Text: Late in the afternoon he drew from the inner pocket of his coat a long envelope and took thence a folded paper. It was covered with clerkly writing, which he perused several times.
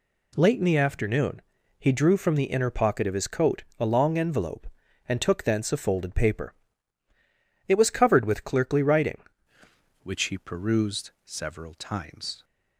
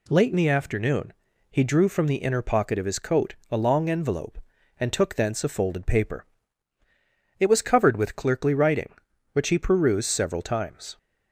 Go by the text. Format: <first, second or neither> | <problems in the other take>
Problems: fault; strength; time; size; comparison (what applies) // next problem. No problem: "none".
second | pauses between "afternoon" and "he"; slight; at 1.4 s; 0.36 s long; slight in the second // pauses between "coat" and "a"; slight; at 3.6 s; 0.16 s long; slight in the second // changes voice at "which"; from 10.0 s on; 2.4 s long